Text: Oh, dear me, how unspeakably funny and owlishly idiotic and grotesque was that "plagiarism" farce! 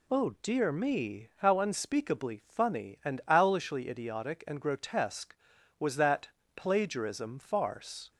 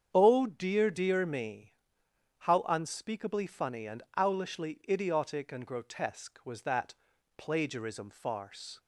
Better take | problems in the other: first | starts louder than the rest; strong; until 1.1 s; 8 dB // says "dear" twice; at 0.8 s // pauses between "and" and "owlishly"; slight; at 4.0 s; 0.16 s long // pauses between "that" and "plagiarism"; at 6.9 s; 0.42 s long; slight in the first

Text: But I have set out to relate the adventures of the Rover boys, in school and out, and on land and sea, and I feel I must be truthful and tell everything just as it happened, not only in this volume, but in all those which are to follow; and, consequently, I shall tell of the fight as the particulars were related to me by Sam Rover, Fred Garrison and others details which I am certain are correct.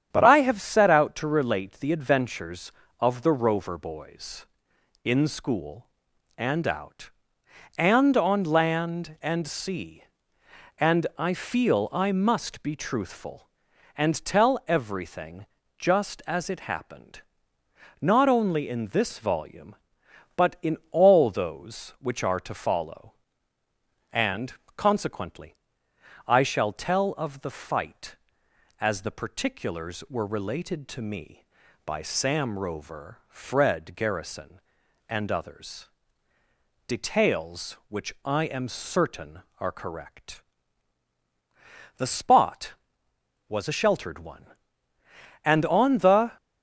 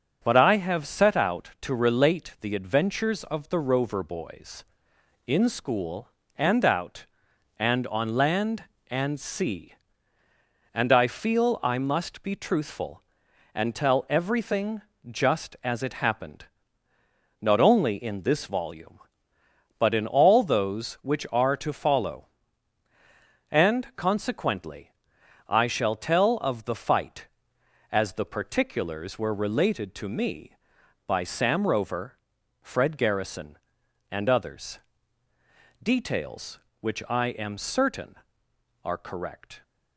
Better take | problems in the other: second | starts louder than the rest; strong; until 1.1 s; 9 dB; also in the second // pauses between "everything" and "just"; slight; at 15.4 s; 0.32 s long; slight in the second // pauses between "others" and "details"; at 35.8 s; 1.0 s long; also in the second // goes on to say "The spot was a sheltered one and on the"; strong; from 41.9 s on; 4.4 s long

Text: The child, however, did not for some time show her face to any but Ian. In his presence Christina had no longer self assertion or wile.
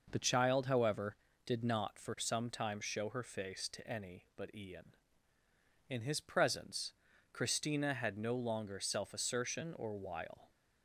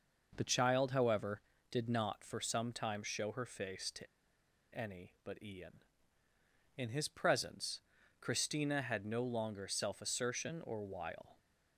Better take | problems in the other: first | pauses between "to" and "any"; noticeable; at 4.0 s; 0.68 s long // pauses between "presence" and "Christina"; at 7.8 s; 0.40 s long; also in the first

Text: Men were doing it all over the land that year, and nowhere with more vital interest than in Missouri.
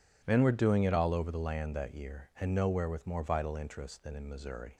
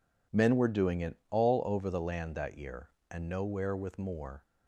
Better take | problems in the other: first | stops before "vital interest than in Missouri"; at 4.4 s

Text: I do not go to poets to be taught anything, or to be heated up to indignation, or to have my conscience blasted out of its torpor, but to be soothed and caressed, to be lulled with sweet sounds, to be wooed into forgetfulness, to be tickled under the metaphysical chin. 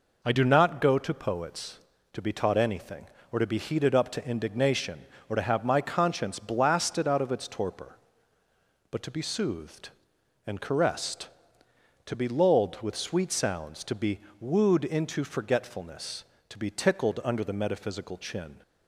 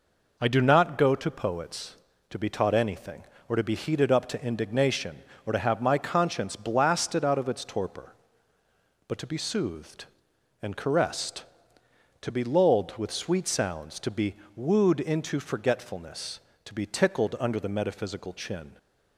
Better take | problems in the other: neither | pauses between "be" and "wooed"; slight; the same in both

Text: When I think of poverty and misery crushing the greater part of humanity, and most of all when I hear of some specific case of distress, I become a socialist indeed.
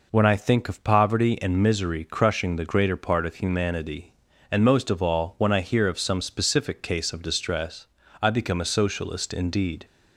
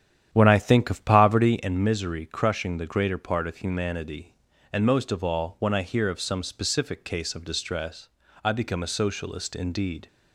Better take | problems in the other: first | starts louder than the rest; strong; until 1.7 s; 10 dB

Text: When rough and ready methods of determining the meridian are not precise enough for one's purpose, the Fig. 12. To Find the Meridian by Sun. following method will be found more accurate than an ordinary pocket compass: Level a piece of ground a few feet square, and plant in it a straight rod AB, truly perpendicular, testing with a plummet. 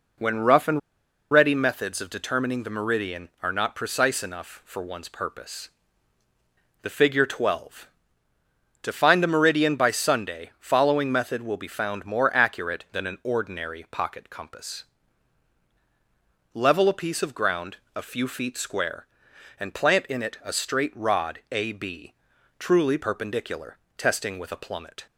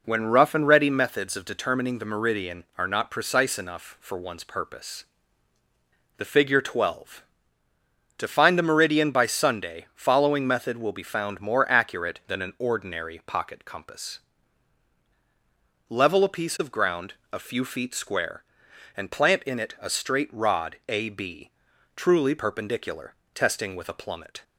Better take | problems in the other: second | pauses between "and" and "ready"; noticeable; at 0.7 s; 0.52 s long // pauses between "ground" and "a"; slight; at 17.7 s; 0.18 s long; slight in the second

